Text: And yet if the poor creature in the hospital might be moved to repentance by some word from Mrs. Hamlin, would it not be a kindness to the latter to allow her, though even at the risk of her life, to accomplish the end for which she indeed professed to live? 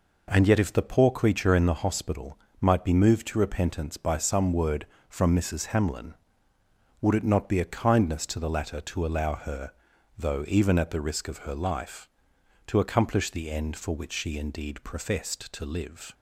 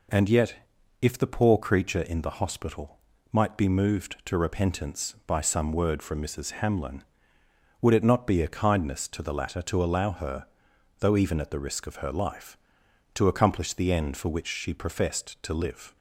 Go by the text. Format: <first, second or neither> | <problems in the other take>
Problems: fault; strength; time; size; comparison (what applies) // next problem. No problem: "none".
first | pauses between "yet" and "if"; noticeable; at 0.5 s; 0.46 s long // pauses between "hospital" and "might"; slight; at 2.9 s; 0.34 s long; slight in the first // skips "indeed"; at 14.7 s